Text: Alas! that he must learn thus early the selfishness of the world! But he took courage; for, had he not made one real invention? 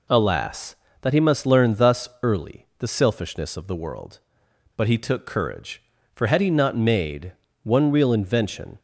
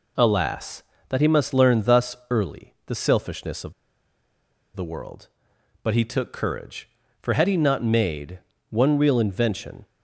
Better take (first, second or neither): first